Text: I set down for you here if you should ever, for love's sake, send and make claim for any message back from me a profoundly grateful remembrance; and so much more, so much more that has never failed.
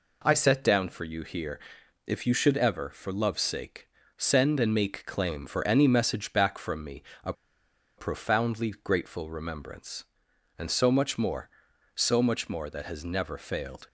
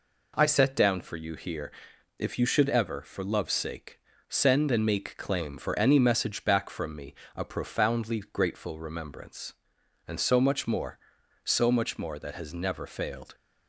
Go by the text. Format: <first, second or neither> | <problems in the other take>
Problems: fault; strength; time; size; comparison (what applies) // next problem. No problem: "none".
second | pauses between "here" and "if"; noticeable; at 1.5 s; 0.48 s long; noticeable in the second // pauses between "me" and "a"; slight; at 7.0 s; 0.22 s long; slight in the second // pauses between "a" and "profoundly"; noticeable; at 7.3 s; 0.65 s long